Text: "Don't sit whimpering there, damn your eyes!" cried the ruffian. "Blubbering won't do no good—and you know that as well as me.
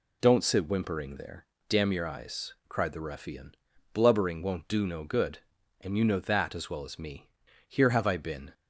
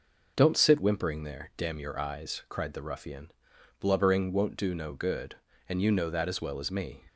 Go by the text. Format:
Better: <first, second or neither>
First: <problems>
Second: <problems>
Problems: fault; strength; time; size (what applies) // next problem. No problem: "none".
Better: second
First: goes on to say "Here have I been"; noticeable; from 7.6 s on; 0.85 s long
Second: none